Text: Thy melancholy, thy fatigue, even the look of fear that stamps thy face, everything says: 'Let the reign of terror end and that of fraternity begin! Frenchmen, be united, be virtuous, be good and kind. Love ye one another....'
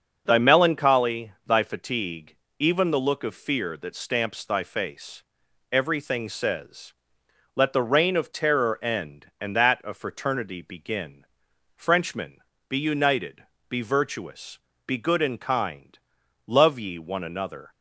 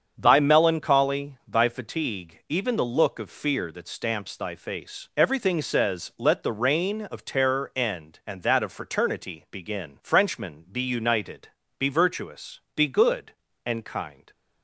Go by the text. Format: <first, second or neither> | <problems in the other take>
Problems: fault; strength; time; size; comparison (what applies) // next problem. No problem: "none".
first | starts louder than the rest; strong; until 1.1 s; 7 dB; also in the first // stops before "Love ye one another"; at 14.3 s